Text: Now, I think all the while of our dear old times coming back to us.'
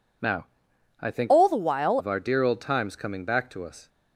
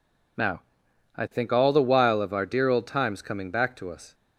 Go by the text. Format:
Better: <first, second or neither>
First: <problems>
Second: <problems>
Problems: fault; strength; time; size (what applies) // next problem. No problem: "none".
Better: second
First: changes voice from "all" to "while"; from 1.2 to 1.9 s; 0.7 s long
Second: none